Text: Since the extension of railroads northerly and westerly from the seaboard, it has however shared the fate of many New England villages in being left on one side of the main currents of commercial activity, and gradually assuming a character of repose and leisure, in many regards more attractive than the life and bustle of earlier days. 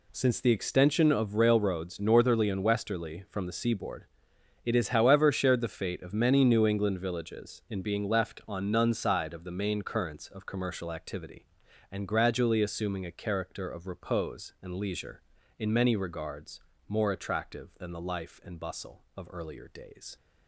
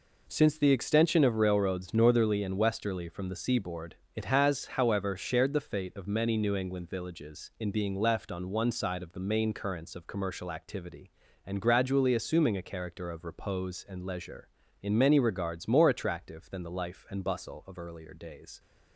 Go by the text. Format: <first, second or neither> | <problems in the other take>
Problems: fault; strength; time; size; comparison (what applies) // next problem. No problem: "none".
second | says "none" for "one"; at 8.7 s // pauses between "regards" and "more"; slight; at 16.6 s; 0.28 s long